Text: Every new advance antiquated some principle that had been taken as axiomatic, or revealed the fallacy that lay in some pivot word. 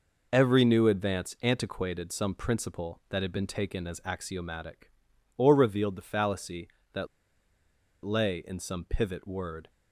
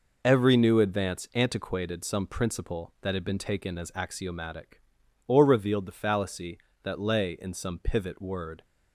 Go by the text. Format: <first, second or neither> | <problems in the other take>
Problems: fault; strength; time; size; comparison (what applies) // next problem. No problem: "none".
second | pauses between "that" and "lay"; at 7.0 s; 0.98 s long